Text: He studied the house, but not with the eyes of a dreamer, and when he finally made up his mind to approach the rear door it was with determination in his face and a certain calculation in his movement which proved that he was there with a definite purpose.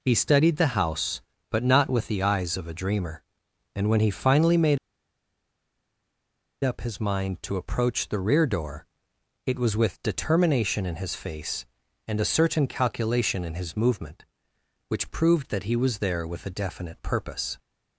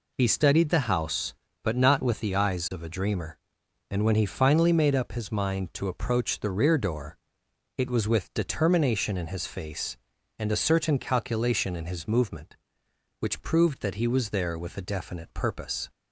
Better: second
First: pauses between "made" and "up"; strong; at 4.7 s; 1.8 s long // pauses between "door" and "it"; noticeable; at 8.8 s; 0.58 s long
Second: pauses between "door" and "it"; noticeable; at 7.1 s; 0.58 s long

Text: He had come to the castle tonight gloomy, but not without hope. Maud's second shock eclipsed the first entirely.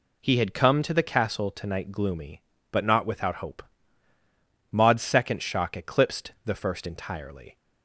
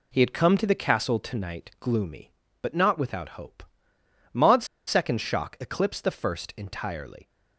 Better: first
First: none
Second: pauses between "Maud's" and "second"; slight; at 4.6 s; 0.20 s long

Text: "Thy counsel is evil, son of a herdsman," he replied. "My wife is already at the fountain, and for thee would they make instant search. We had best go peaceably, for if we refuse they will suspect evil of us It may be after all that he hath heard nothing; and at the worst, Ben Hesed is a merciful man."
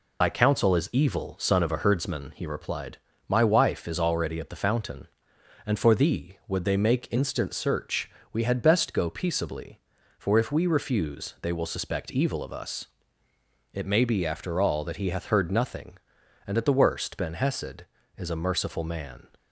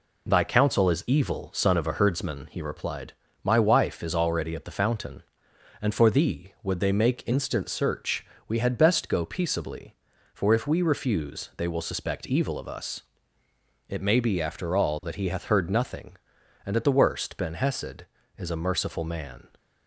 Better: second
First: loses the start of "Thy"; at 0.2 s; 85 ms // pauses between "us" and "It"; noticeable; at 12.8 s; 0.86 s long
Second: pauses between "us" and "It"; noticeable; at 13.0 s; 0.86 s long

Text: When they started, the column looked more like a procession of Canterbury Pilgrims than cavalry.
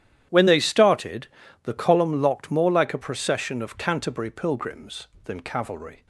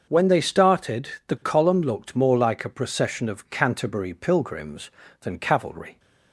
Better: second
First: starts louder than the rest; strong; until 1.6 s; 11 dB // says "locked" for "looked"; at 2.2 s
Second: starts louder than the rest; until 1.1 s; 6.5 dB

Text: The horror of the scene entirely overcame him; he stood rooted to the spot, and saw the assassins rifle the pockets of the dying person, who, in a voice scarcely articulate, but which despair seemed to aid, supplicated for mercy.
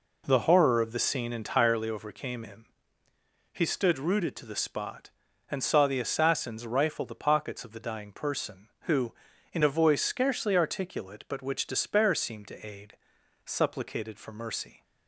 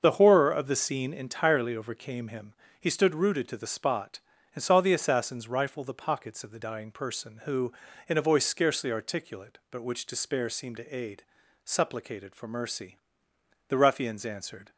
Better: first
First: none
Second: starts louder than the rest; until 1.0 s; 6.5 dB // goes on to say "The ruffians answered"; noticeable; from 13.6 s on; 1.0 s long

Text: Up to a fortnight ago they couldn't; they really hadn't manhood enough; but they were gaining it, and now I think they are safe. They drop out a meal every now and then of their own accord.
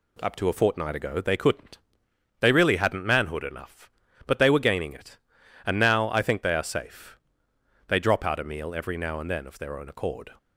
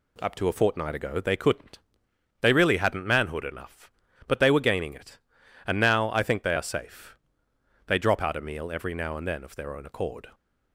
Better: neither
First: none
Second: none

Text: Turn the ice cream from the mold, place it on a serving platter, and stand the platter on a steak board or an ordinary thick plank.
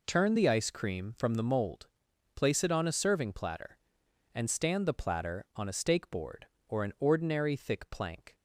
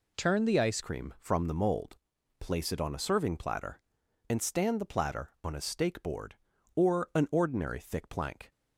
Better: first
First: none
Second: changes voice at "cream"; from 0.8 s on; 7.7 s long

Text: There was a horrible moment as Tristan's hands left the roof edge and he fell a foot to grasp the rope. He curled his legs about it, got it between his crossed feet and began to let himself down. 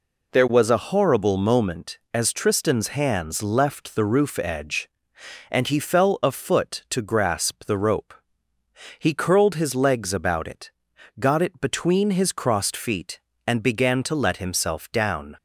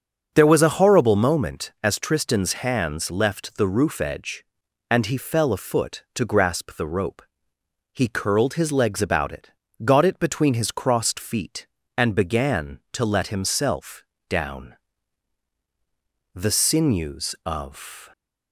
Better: first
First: none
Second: starts louder than the rest; until 1.3 s; 6.5 dB // pauses between "himself" and "down"; slight; at 14.0 s; 0.26 s long // goes on to say "The sinews of"; strong; from 16.3 s on; 1.7 s long

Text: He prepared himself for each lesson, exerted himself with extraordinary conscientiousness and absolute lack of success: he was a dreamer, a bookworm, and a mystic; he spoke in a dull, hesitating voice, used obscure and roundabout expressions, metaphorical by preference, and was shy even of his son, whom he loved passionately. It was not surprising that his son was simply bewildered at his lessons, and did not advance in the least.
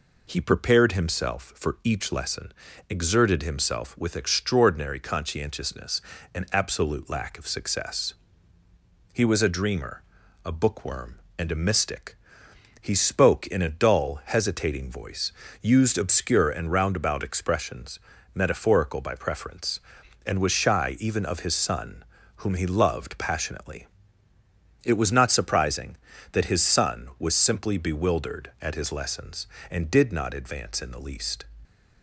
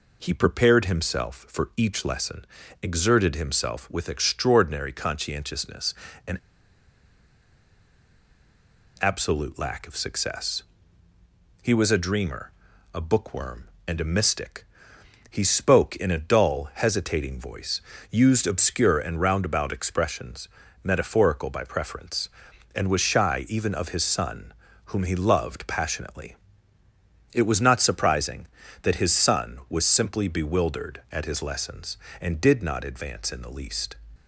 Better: first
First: none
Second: pauses between "and" and "absolute"; strong; at 6.3 s; 2.6 s long

